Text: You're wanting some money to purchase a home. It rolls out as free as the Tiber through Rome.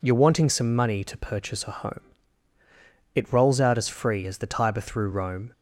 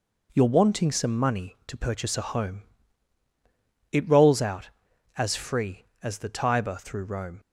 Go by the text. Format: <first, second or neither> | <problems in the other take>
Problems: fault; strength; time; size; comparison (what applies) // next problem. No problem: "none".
neither | none